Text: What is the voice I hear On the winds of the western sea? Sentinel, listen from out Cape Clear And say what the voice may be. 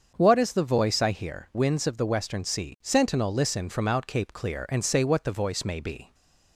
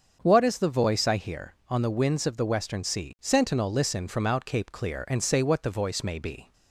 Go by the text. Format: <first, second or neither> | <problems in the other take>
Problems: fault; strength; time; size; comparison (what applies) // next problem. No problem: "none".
second | starts louder than the rest; until 1.1 s; 7 dB; also in the second // skips "On the"; at 1.5 s